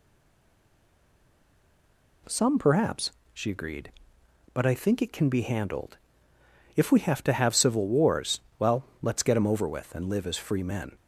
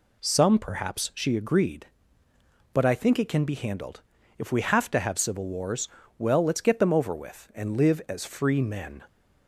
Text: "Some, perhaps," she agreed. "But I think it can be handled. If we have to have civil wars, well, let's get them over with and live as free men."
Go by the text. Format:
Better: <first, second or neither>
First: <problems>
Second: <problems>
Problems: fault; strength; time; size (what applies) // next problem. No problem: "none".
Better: second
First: stays silent before the first word; until 2.2 s; 2.2 s long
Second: none